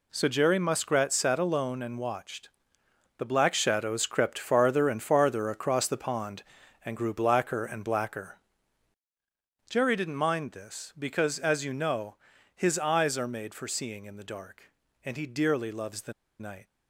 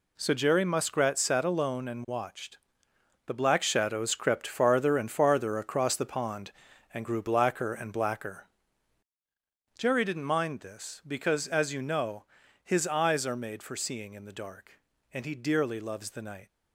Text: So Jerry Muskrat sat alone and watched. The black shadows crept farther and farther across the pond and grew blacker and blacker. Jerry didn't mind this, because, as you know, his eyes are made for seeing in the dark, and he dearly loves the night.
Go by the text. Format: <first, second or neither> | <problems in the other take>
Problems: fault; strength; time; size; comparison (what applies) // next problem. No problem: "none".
second | pauses between "the" and "night"; slight; at 16.1 s; 0.27 s long